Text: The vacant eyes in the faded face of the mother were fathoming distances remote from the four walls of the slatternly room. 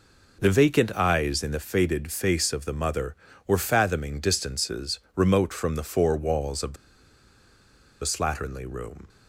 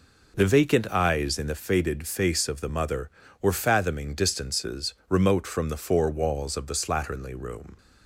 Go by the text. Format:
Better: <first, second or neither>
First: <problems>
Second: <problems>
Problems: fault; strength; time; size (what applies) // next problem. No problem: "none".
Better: second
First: pauses between "the" and "slatternly"; strong; at 6.7 s; 1.2 s long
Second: none